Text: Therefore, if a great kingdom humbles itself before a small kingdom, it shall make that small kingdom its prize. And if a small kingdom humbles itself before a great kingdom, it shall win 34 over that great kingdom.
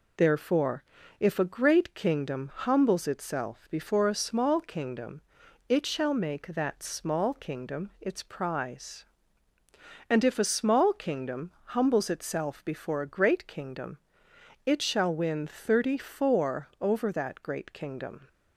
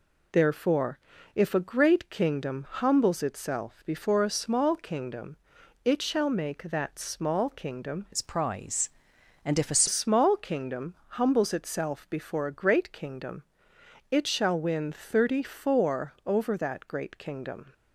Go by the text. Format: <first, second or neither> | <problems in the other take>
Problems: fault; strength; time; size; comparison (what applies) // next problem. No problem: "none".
first | changes voice from "its" to "a"; from 8.1 to 9.8 s; 1.7 s long